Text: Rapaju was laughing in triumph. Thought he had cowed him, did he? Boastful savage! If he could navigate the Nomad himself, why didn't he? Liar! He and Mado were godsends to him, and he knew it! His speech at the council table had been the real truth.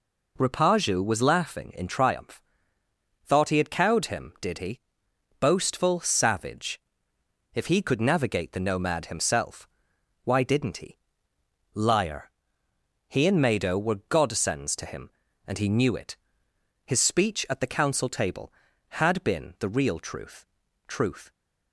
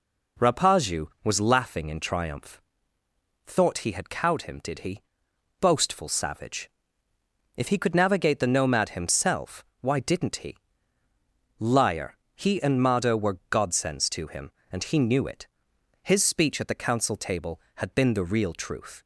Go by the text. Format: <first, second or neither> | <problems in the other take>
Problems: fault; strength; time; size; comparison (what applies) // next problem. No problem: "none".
second | says "truth" twice; at 20.8 s